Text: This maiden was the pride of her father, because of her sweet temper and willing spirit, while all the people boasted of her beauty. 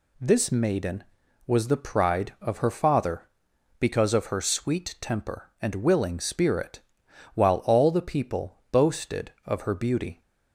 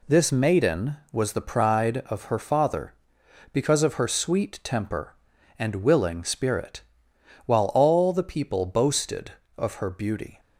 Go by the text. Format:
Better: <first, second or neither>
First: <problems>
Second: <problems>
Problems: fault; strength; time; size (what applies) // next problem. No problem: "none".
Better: neither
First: none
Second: none